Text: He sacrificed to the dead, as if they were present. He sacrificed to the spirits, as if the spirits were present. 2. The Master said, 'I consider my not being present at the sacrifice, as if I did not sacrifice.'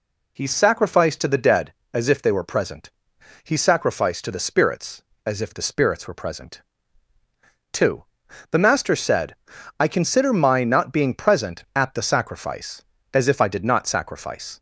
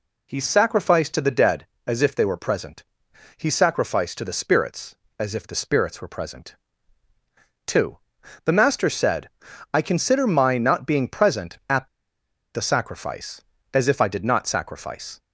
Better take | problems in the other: first | pauses between "at" and "the"; noticeable; at 11.8 s; 0.66 s long

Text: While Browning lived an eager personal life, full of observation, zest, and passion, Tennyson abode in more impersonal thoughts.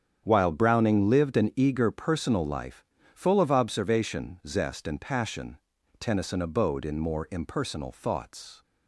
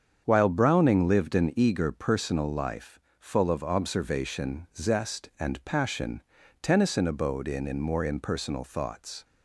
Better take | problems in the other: first | starts louder than the rest; strong; until 1.2 s; 7.5 dB; strong in the first // says "in" twice; at 7.6 s

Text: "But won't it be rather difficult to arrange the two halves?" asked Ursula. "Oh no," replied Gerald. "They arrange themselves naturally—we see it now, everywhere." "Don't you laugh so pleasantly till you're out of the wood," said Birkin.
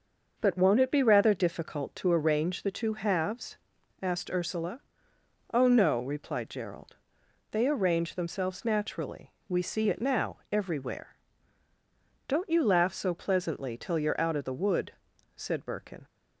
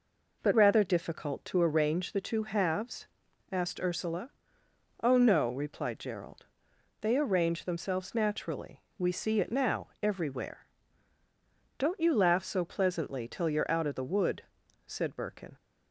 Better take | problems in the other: first | skips "won't it be"; at 0.5 s

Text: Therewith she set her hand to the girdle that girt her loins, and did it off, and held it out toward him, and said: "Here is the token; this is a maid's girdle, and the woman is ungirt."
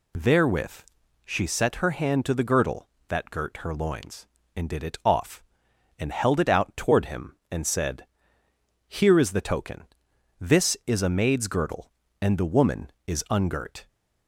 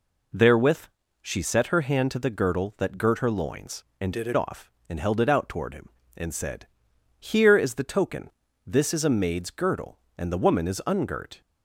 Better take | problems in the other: first | pauses between "Therewith" and "she"; slight; at 0.8 s; 0.36 s long; also in the first // changes voice from "did" to "it"; from 4.1 to 4.3 s; 0.2 s long

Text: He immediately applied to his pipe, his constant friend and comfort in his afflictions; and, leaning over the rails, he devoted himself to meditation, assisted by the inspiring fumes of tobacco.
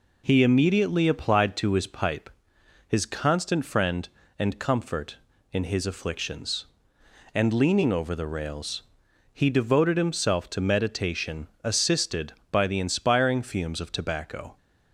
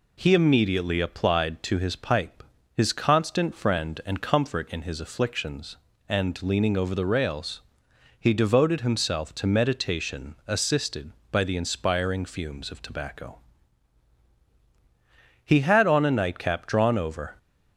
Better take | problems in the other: first | goes on to say "He had on a nightcap drawn over"; strong; from 15.4 s on; 1.9 s long

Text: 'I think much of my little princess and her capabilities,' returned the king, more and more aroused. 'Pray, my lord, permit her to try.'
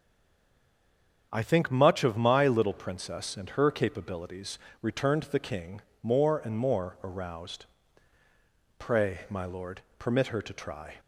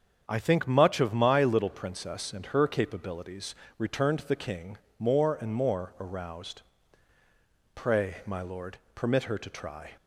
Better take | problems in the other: second | stays silent before the first word; noticeable; until 1.3 s; 1.3 s long // starts louder than the rest; strong; until 2.3 s; 7.5 dB; strong in the second

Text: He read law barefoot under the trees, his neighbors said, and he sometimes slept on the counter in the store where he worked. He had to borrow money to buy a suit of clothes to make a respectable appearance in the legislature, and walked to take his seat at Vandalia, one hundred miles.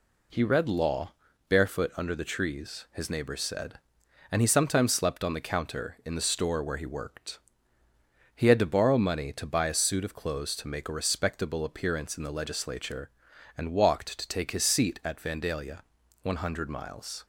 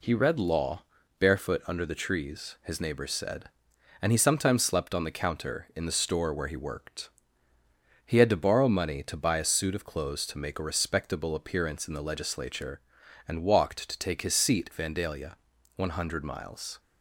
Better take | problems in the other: first | pauses between "law" and "barefoot"; slight; at 0.8 s; 0.36 s long; slight in the first // skips "at"; at 14.7 s

